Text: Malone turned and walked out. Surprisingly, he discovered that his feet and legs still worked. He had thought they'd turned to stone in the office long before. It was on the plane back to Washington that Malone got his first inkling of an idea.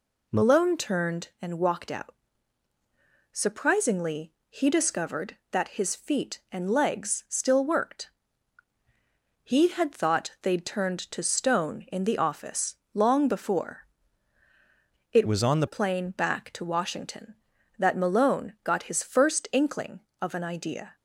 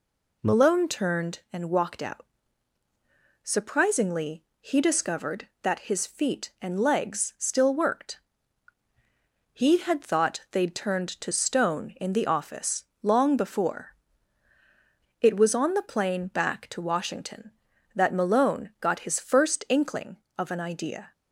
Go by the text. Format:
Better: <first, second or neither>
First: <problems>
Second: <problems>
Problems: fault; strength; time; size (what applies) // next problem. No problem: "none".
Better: second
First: pauses between "office" and "long"; slight; at 12.7 s; 0.16 s long // changes voice from "was" to "the"; from 15.2 to 15.6 s; 0.4 s long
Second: pauses between "office" and "long"; slight; at 12.8 s; 0.16 s long